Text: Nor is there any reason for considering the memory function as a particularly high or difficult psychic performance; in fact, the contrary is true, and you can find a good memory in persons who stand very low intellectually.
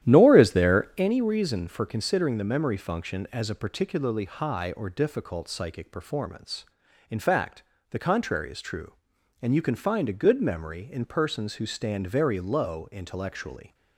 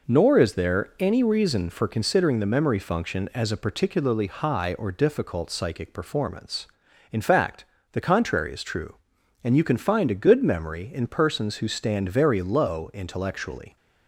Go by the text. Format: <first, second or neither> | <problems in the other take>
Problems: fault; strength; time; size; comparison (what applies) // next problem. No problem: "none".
second | starts louder than the rest; strong; until 1.2 s; 11.5 dB